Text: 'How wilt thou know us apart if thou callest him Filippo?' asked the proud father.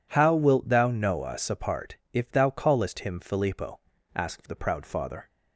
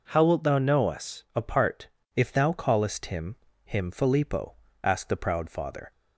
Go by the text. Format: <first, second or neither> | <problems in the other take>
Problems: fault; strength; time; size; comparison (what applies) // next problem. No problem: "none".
first | pauses between "apart" and "if"; slight; at 1.8 s; 0.28 s long; slight in the first // says "him" twice; at 3.6 s